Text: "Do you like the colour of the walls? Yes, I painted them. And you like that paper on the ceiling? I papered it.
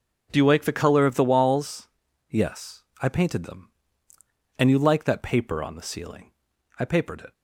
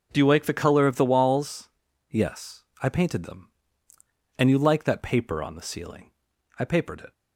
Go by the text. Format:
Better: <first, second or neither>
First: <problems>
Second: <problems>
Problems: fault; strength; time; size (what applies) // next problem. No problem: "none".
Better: neither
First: none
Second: none